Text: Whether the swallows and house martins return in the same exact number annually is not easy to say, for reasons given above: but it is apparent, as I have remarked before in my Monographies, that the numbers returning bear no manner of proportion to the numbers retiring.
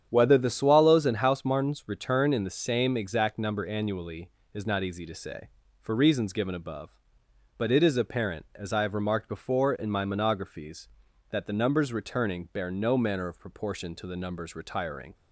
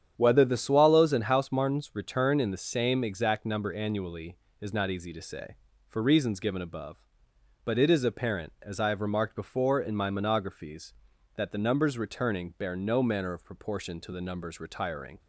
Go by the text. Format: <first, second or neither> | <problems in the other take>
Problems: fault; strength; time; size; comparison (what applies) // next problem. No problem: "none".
neither | starts louder than the rest; strong; the same in both